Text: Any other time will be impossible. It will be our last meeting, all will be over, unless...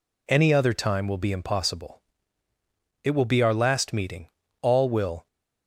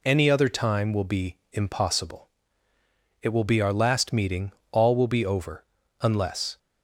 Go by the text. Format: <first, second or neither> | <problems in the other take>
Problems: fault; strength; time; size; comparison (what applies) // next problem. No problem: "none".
second | stops before "be over unless"; at 5.2 s